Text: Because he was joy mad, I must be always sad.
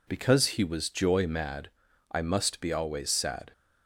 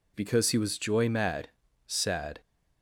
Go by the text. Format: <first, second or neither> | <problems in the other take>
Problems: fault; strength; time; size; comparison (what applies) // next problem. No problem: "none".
first | skips "I must be always"; at 1.6 s